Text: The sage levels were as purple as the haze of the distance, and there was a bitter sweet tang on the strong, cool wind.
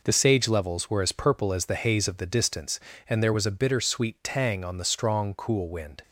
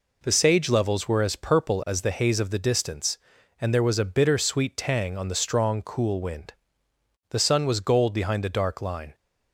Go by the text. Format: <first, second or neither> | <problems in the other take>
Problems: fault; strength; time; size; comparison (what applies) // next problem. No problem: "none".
first | goes on to say "The sun was gold behind the dark line"; strong; from 7.2 s on; 1.8 s long